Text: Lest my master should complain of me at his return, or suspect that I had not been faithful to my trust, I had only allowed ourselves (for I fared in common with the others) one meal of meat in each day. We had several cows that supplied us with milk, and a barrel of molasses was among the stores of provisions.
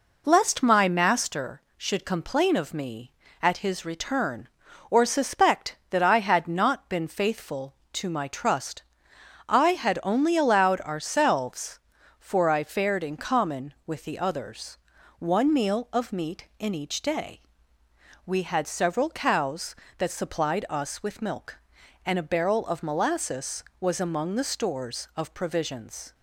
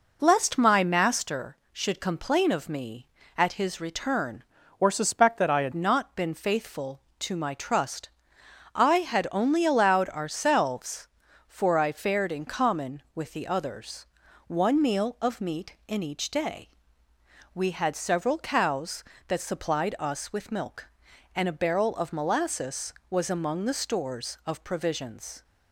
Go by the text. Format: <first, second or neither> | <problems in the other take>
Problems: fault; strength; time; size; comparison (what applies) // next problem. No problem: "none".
first | changes voice from "or" to "had"; from 4.7 to 5.7 s; 1.0 s long